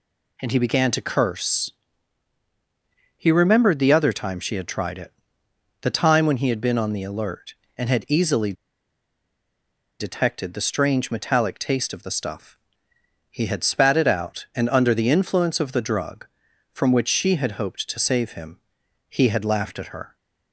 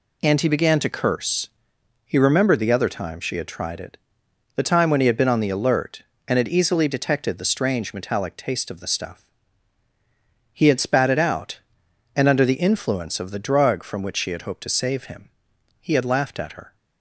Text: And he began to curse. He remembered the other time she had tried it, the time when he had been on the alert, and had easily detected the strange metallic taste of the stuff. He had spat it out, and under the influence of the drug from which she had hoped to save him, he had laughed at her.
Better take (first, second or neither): second